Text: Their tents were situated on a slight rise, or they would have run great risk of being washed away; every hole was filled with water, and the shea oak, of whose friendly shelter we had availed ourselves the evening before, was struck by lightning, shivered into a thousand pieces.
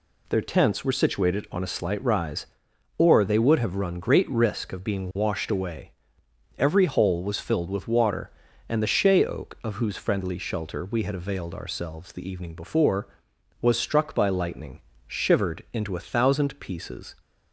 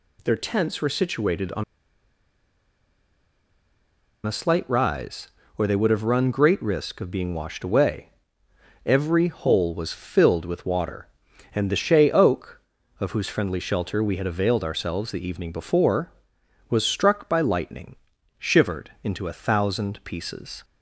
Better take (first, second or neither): first